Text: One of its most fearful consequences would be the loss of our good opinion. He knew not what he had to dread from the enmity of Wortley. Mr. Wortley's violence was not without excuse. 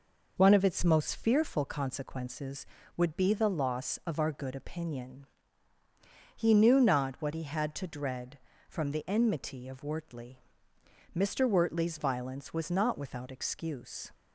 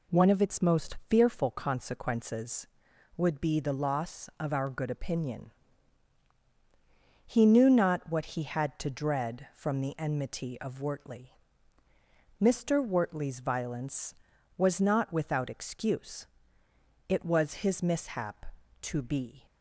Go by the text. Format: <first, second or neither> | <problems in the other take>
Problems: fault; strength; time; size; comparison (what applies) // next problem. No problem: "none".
first | goes on to say "It was his mishap to be"; strong; from 17.0 s on; 2.3 s long